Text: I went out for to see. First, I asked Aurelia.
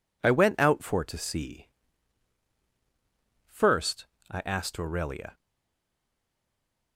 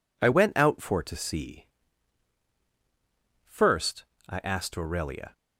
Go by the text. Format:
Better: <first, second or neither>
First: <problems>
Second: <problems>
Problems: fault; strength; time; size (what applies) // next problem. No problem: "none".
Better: second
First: stays silent after the last word; noticeable; from 5.3 s on; 1.6 s long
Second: none